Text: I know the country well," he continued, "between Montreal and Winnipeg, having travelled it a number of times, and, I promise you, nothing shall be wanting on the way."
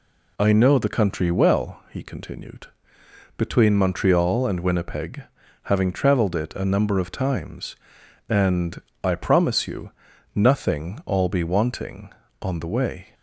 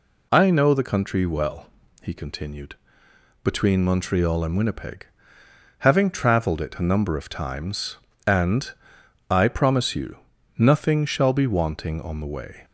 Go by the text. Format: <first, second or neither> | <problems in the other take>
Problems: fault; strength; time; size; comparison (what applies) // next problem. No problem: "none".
second | says "all" for "shall"; at 11.0 s